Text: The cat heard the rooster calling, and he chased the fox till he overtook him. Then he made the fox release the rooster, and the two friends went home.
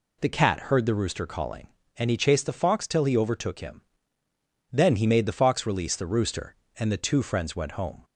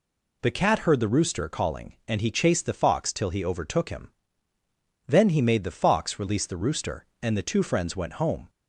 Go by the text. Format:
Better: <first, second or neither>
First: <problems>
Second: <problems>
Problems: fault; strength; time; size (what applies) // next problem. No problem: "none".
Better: neither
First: none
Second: none